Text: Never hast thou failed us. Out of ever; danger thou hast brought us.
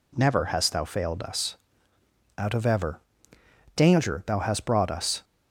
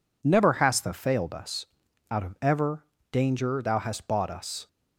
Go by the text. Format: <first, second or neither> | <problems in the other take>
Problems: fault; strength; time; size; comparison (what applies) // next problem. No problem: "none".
first | says "bought" for "brought"; at 4.0 s